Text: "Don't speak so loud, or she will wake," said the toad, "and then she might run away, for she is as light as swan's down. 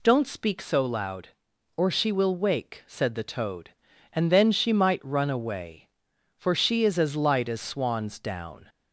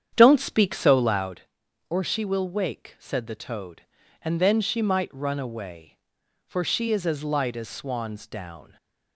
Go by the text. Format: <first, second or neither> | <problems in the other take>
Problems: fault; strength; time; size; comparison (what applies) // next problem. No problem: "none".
first | starts louder than the rest; strong; until 1.5 s; 9 dB